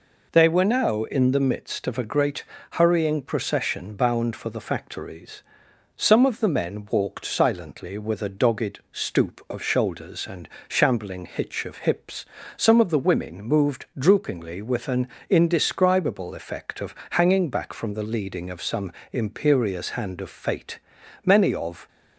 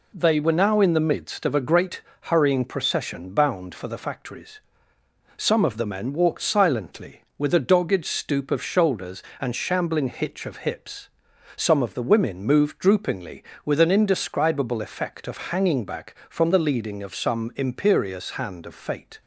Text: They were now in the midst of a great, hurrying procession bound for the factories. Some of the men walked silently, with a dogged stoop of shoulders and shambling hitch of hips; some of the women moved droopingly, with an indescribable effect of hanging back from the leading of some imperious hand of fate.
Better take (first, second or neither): second